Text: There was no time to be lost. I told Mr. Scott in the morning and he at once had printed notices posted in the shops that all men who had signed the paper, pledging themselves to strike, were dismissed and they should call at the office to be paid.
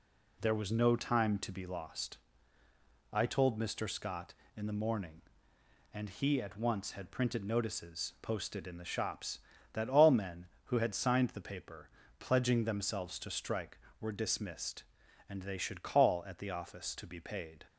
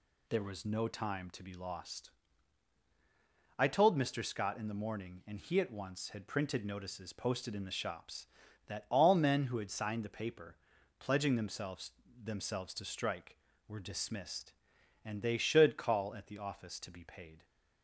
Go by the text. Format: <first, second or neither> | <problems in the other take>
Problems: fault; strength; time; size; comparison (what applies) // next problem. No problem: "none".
first | says "themselves" twice; at 12.2 s